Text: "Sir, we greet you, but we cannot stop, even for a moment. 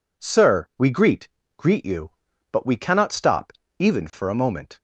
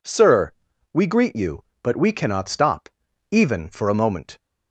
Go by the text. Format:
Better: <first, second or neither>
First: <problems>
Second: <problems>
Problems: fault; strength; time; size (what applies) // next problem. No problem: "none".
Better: second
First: says "greet" twice; at 1.5 s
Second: none